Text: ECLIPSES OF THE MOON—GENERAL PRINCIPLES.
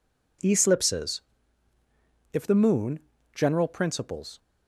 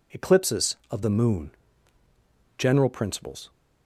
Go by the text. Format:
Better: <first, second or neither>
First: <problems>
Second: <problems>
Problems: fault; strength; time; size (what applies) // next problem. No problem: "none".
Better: second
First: says "If" for "OF"; at 2.3 s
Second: none